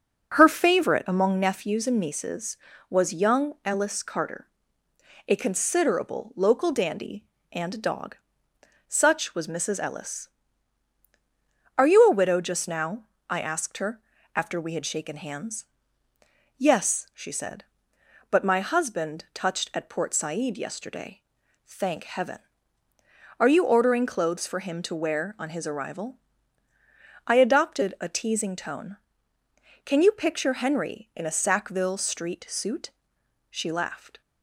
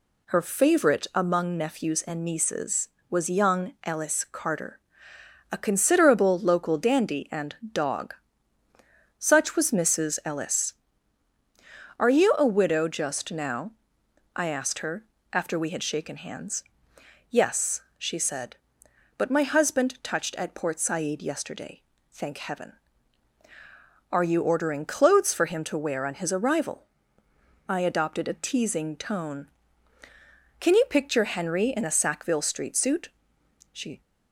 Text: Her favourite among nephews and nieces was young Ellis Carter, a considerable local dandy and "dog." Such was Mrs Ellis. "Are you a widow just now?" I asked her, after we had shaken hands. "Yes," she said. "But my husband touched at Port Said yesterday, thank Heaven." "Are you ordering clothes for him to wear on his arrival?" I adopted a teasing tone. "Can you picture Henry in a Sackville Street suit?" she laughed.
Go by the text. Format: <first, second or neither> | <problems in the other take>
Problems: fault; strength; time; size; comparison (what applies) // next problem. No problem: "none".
first | pauses between "and" and "dog"; slight; at 7.5 s; 0.18 s long // stops before "laughed"; at 34.0 s